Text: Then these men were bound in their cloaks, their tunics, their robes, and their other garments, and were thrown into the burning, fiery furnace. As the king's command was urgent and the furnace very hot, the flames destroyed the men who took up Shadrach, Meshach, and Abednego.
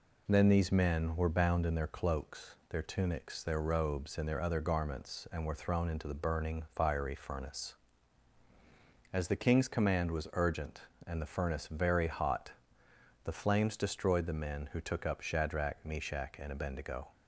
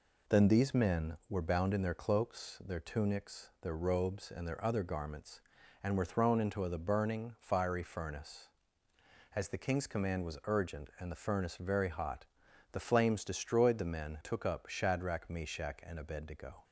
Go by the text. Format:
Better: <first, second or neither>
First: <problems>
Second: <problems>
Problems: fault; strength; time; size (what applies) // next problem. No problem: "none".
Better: first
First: none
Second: skips "who"; at 14.1 s